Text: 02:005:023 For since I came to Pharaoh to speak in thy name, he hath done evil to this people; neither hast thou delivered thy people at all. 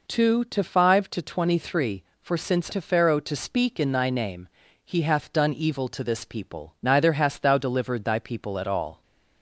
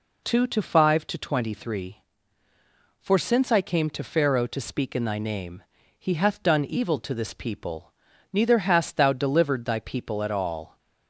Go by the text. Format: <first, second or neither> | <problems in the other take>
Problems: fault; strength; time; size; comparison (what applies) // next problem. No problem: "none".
second | skips "I came"; at 2.7 s